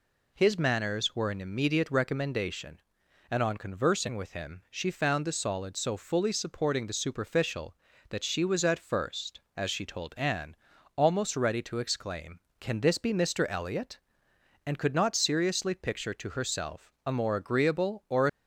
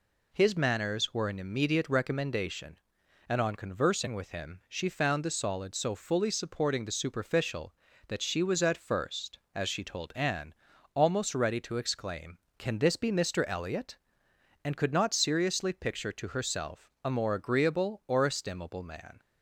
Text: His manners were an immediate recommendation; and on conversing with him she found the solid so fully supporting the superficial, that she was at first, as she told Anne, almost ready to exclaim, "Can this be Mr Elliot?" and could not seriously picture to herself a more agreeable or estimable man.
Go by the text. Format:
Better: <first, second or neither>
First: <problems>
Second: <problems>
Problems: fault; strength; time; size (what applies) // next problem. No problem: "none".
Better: second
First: stops before "estimable man"; at 18.2 s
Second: none